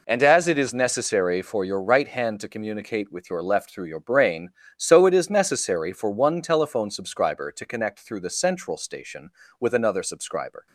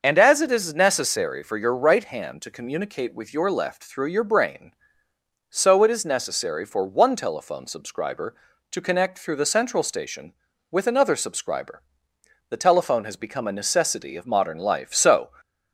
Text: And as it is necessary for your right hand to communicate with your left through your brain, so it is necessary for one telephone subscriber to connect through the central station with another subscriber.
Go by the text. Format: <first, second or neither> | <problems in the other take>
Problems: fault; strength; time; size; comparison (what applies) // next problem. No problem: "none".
first | starts louder than the rest; until 1.0 s; 6 dB // goes on to say "The telephone has become a necessity of modern life so"; strong; from 12.4 s on; 2.8 s long